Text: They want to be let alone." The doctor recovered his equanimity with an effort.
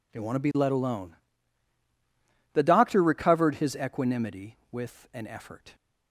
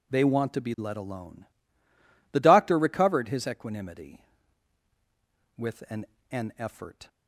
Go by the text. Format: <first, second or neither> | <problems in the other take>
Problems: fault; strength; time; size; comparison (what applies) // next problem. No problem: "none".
first | says "an" twice; at 6.2 s